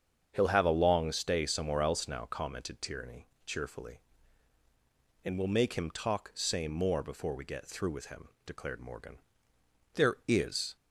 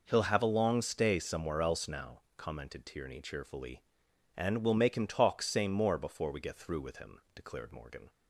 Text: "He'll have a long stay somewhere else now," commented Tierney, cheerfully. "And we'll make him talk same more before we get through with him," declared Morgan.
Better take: second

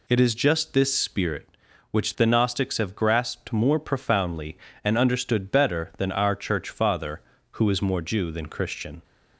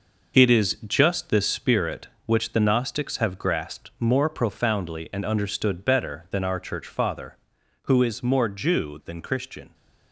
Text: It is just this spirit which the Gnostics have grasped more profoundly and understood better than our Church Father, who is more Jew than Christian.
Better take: first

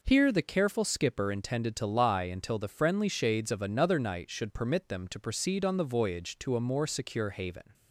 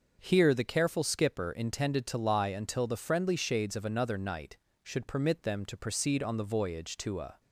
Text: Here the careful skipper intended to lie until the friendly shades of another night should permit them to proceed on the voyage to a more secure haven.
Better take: first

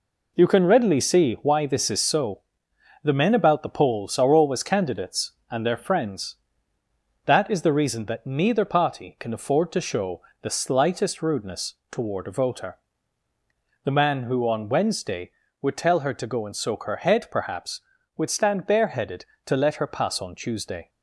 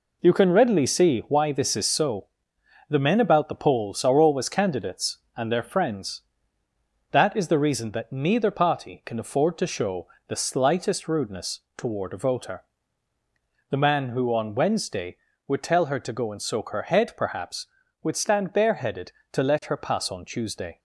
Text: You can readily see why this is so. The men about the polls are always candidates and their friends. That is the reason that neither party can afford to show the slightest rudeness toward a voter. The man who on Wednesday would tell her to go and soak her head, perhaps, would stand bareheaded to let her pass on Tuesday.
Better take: neither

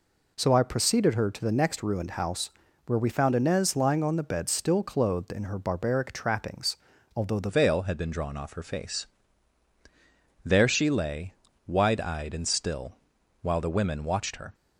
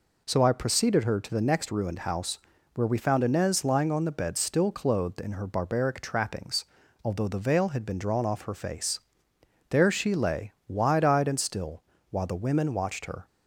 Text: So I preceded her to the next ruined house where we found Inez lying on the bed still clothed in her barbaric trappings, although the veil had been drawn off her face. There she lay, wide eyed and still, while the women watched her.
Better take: second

